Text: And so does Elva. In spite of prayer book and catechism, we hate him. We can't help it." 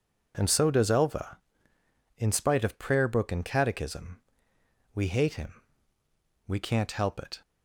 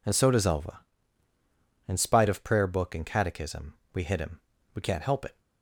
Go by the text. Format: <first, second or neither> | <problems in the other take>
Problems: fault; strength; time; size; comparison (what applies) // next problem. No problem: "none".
first | says "hit" for "hate"; at 4.0 s